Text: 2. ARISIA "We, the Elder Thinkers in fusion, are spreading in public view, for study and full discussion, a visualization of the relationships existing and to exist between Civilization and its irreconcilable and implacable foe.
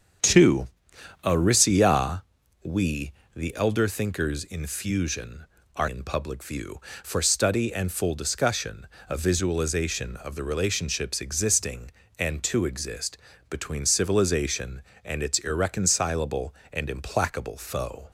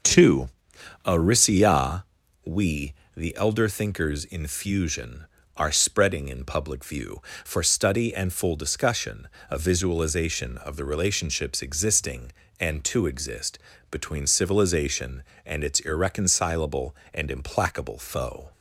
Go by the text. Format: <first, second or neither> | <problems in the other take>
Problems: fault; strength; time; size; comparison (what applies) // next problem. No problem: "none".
second | starts louder than the rest; strong; until 1.7 s; 7.5 dB; also in the second // pauses between "ARISIA" and "We"; at 2.2 s; 0.42 s long; also in the second // skips "spreading"; at 5.8 s // pauses between "exist" and "between"; slight; at 13.1 s; 0.32 s long; slight in the second